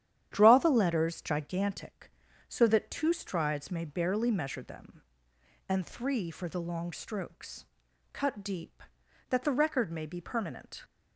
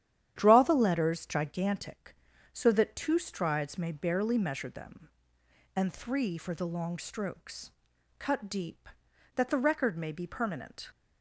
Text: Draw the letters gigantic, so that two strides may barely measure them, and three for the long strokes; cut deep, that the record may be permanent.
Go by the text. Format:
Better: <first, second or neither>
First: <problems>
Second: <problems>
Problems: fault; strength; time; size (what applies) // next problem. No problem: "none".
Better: neither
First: starts louder than the rest; strong; until 1.3 s; 10 dB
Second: starts louder than the rest; strong; until 1.3 s; 10 dB